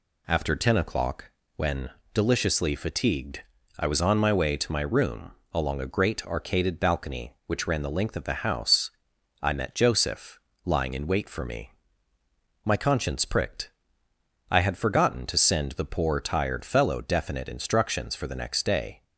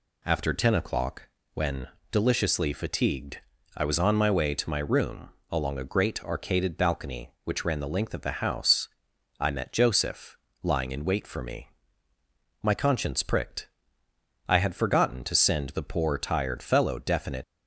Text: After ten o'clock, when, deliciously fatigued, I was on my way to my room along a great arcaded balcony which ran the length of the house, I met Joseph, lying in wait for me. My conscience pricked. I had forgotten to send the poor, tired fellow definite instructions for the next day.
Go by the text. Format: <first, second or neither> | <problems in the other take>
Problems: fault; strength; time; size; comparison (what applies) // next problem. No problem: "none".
first | pauses between "room" and "along"; slight; at 5.3 s; 0.20 s long; slight in the first // stops before "instructions for the next day"; at 17.4 s